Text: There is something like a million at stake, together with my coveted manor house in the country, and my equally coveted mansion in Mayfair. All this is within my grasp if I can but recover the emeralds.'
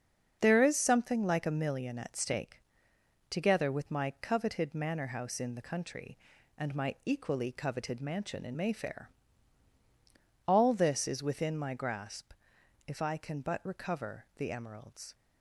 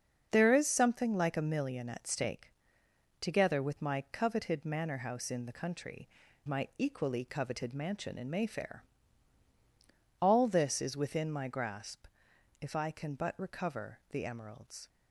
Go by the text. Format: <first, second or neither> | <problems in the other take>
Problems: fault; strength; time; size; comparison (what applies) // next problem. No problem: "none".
first | starts louder than the rest; until 1.3 s; 6.5 dB; also in the first // skips "and"; at 6.2 s // pauses between "grasp" and "if"; noticeable; at 12.0 s; 0.54 s long; noticeable in the first